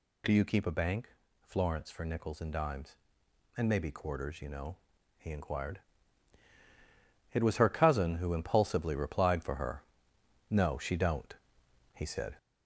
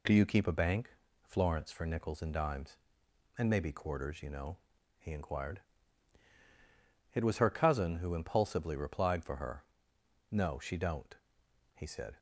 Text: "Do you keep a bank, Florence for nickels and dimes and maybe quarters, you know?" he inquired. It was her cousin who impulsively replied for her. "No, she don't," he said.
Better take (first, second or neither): second